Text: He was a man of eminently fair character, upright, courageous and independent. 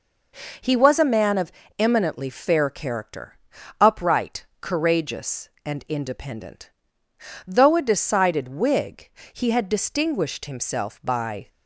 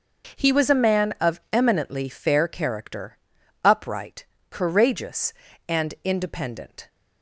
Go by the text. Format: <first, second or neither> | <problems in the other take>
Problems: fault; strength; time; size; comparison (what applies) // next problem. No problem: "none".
second | pauses between "of" and "eminently"; slight; at 1.5 s; 0.26 s long // goes on to say "Though a decided Whig he had distinguished himself by"; strong; from 7.4 s on; 4.0 s long